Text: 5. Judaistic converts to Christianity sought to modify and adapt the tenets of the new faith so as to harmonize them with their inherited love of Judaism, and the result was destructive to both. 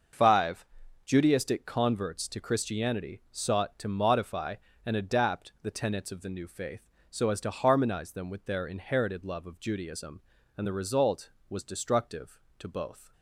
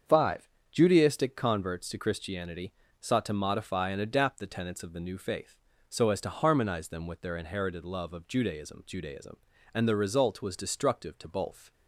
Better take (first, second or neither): first